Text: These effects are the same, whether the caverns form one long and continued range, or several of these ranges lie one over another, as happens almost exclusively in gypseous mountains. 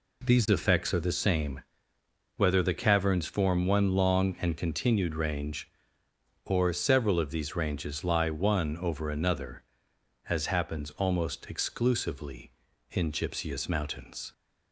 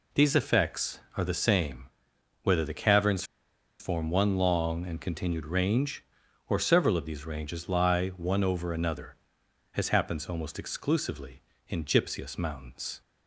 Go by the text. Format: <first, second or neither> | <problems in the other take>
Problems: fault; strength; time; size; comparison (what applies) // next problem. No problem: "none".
first | pauses between "caverns" and "form"; noticeable; at 3.2 s; 0.56 s long